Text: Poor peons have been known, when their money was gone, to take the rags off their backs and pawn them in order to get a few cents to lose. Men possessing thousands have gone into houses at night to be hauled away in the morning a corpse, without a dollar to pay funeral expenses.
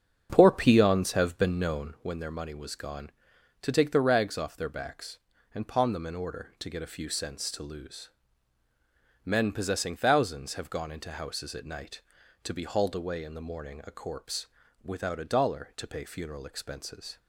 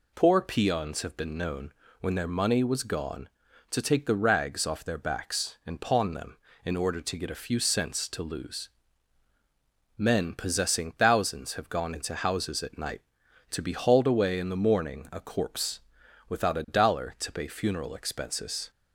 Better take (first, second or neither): second